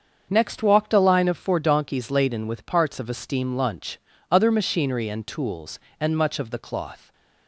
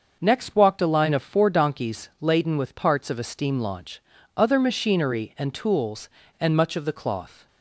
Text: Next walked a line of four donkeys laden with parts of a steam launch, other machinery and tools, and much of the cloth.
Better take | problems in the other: second | starts louder than the rest; until 1.3 s; 7 dB; also in the second // says "lunch" for "launch"; at 3.5 s

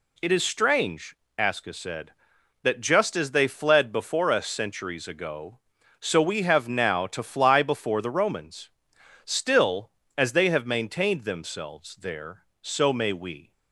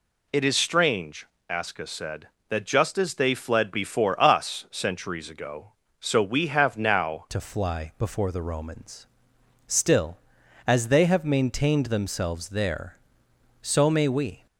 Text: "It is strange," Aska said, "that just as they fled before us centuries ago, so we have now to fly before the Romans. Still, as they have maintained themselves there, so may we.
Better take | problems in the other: first | changes voice at "to"; from 7.2 s on; 7.2 s long

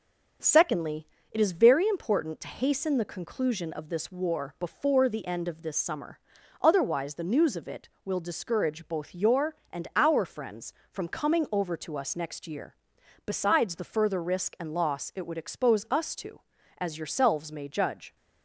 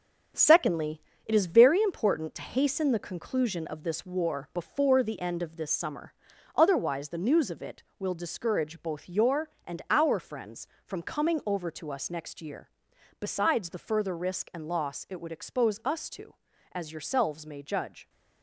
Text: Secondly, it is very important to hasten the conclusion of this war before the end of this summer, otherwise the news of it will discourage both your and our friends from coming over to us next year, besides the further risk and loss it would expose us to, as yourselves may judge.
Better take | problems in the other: first | gets quieter; throughout; 6.5 dB // starts louder than the rest; strong; until 1.6 s; 7.5 dB; noticeable in the first

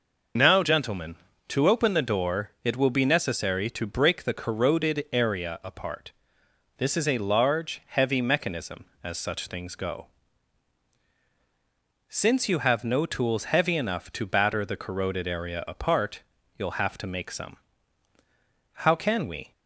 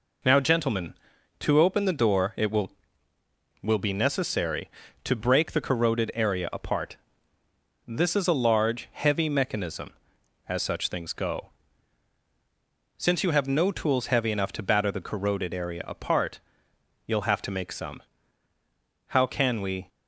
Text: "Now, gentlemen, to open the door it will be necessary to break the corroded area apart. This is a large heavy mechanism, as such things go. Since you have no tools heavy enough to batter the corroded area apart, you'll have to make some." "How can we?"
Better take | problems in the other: first | says "will" twice; at 3.6 s

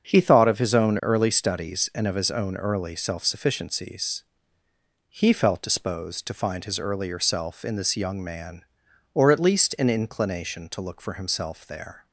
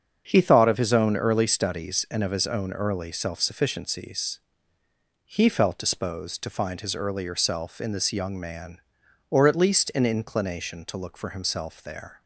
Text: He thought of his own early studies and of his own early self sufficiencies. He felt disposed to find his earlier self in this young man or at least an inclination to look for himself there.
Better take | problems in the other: neither | starts louder than the rest; the same in both

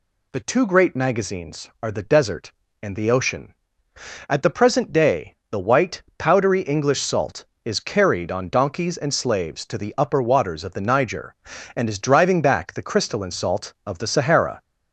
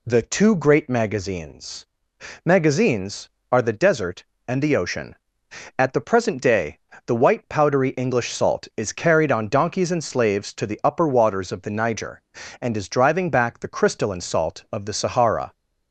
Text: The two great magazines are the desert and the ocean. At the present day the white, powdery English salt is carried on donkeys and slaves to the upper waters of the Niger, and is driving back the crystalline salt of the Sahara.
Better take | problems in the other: first | says "magazines" twice; at 2.4 s // pauses between "day" and "the"; slight; at 6.7 s; 0.30 s long; slight in the first

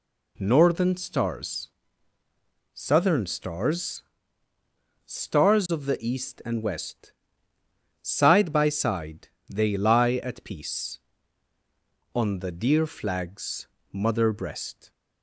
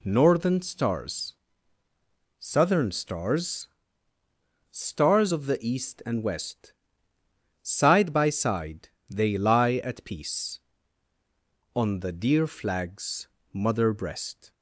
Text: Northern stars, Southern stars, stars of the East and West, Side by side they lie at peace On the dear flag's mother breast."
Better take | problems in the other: neither | pauses between "side" and "they"; slight; the same in both // pauses between "flag's" and "mother"; slight; the same in both

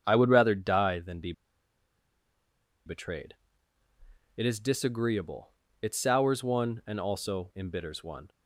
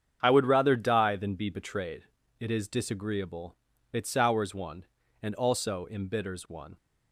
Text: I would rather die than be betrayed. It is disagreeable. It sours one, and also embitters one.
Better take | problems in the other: second | starts louder than the rest; strong; until 1.0 s; 7 dB; strong in the second // pauses between "be" and "betrayed"; strong; at 1.3 s; 1.5 s long

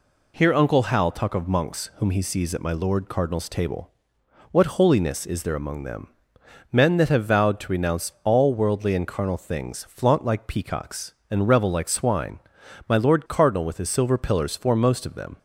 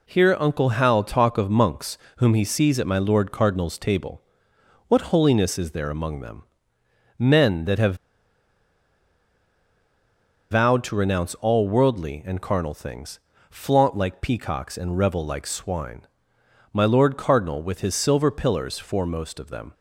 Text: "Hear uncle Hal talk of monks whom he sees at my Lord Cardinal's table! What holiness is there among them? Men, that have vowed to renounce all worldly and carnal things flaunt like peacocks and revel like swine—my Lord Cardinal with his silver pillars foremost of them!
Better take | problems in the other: first | pauses between "monks" and "whom"; slight; at 1.9 s; 0.20 s long // pauses between "have" and "vowed"; strong; at 7.9 s; 2.5 s long // pauses between "things" and "flaunt"; slight; at 13.1 s; 0.30 s long

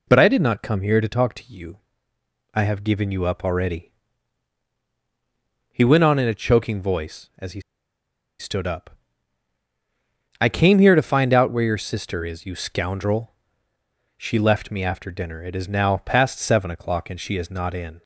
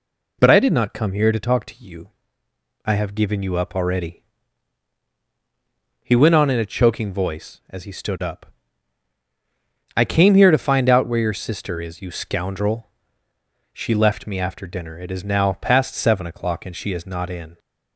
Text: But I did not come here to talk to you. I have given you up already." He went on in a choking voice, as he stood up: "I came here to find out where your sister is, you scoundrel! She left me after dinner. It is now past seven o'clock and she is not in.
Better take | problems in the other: second | pauses between "he" and "stood"; noticeable; at 7.5 s; 0.80 s long

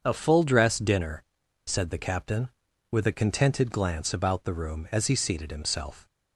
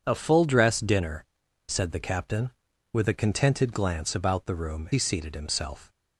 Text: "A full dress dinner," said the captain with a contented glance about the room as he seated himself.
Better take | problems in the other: first | starts louder than the rest; strong; until 1.0 s; 7.5 dB; also in the first // skips "as"; at 4.9 s

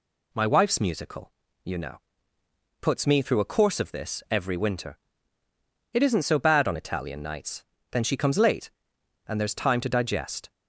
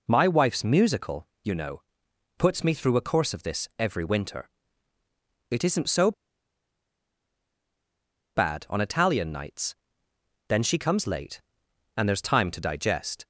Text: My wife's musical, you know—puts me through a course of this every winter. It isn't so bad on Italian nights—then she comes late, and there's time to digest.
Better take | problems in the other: first | pauses between "so" and "bad"; strong; at 6.1 s; 2.2 s long

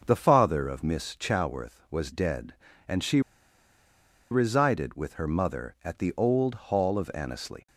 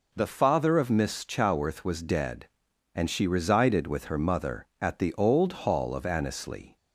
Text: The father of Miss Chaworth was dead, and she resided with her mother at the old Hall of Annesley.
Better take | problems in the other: second | pauses between "she" and "resided"; at 3.2 s; 1.1 s long

